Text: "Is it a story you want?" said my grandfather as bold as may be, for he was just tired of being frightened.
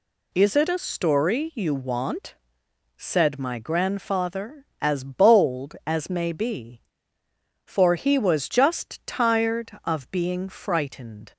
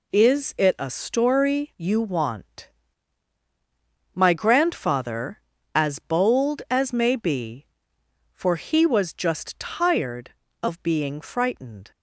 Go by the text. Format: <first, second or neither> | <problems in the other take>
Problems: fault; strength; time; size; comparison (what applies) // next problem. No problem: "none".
first | skips "said"; at 3.4 s